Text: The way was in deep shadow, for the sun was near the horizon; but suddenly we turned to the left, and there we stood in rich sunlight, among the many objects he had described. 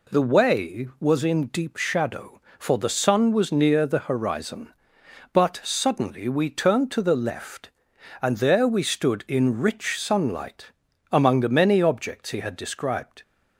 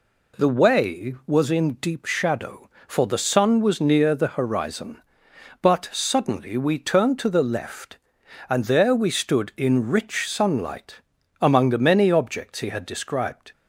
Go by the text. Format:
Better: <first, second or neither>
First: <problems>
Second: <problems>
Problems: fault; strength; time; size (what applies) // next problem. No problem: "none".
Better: neither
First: none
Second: none